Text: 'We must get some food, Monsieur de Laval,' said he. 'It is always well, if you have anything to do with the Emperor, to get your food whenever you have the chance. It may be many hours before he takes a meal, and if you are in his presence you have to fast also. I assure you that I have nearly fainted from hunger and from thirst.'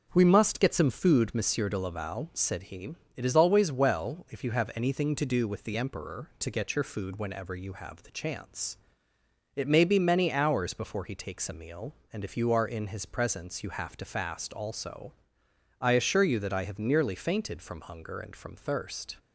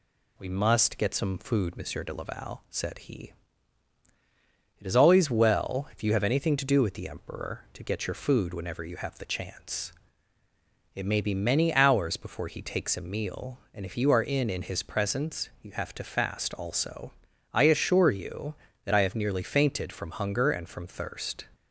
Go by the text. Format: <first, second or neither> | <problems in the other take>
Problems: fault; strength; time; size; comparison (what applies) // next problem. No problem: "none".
first | says "in" twice; at 14.5 s